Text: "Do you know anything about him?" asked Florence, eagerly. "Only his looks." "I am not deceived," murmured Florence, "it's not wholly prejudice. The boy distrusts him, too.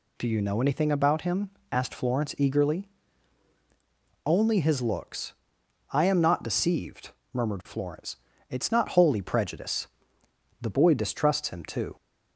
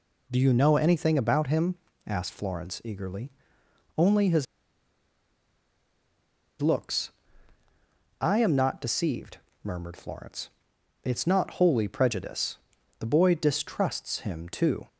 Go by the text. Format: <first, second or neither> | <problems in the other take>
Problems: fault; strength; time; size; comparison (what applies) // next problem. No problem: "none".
first | pauses between "his" and "looks"; strong; at 4.4 s; 2.1 s long